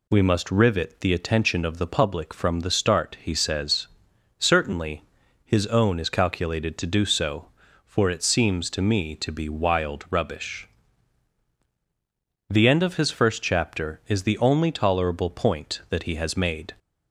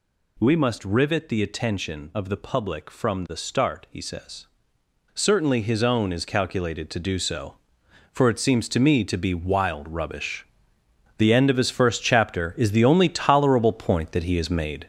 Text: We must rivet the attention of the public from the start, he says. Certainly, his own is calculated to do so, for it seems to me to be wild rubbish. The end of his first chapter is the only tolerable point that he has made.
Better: first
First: none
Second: gets louder; throughout; 6 dB

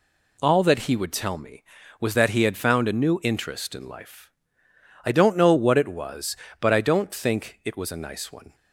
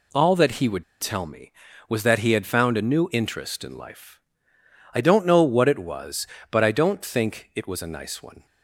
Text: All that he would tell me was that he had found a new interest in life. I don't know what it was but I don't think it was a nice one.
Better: first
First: none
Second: pauses between "would" and "tell"; slight; at 0.8 s; 0.17 s long

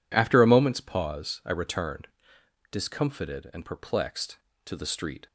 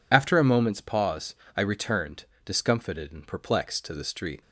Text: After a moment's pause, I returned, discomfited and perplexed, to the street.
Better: first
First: none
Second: loses the start of "After"; at 0.1 s; 35 ms

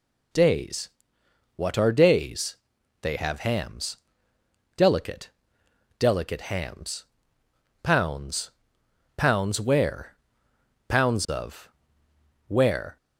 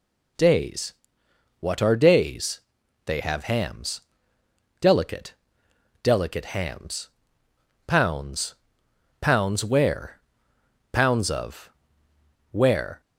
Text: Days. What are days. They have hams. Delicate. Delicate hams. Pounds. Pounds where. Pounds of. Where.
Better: neither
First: none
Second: none

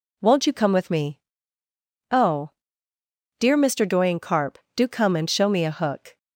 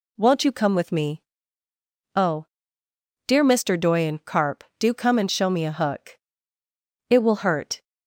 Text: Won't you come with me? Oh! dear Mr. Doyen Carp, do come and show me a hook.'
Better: first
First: none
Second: goes on to say "It will hurt"; noticeable; from 7.1 s on; 0.72 s long

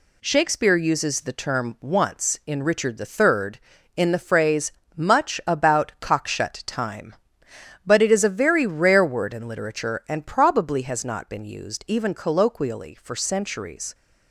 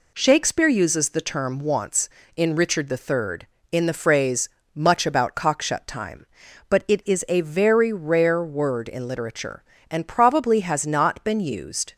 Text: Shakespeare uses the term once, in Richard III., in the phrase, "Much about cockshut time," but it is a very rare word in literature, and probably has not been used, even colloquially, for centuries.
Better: first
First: none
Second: stops before "even colloquially for centuries"; at 11.9 s

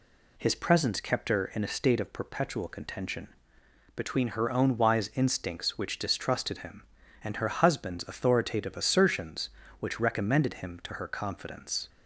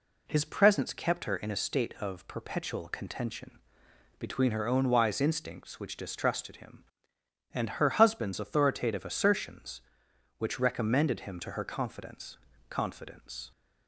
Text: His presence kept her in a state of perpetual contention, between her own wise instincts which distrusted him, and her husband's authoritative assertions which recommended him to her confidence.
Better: first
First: none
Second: says "confidence" twice; at 12.6 s

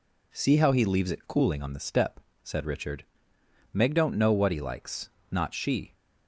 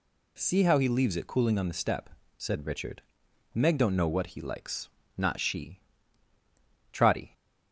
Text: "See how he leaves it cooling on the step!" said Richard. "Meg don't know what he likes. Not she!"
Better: first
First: none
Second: goes on to say "Trotty"; slight; from 6.9 s on; 0.40 s long

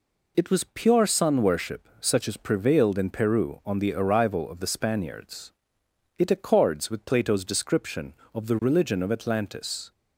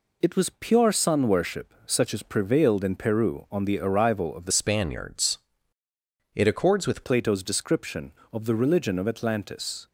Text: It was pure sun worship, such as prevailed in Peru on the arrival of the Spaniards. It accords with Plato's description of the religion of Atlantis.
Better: first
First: none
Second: changes voice from "Spaniards" to "with"; from 4.5 to 7.0 s; 2.5 s long

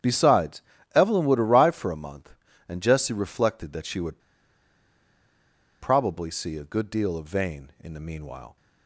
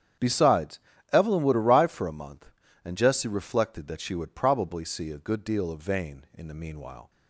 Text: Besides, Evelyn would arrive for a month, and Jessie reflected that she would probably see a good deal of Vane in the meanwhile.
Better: second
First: starts louder than the rest; strong; until 1.3 s; 9 dB // pauses between "would" and "probably"; strong; at 4.1 s; 1.6 s long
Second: starts louder than the rest; strong; until 1.5 s; 9 dB

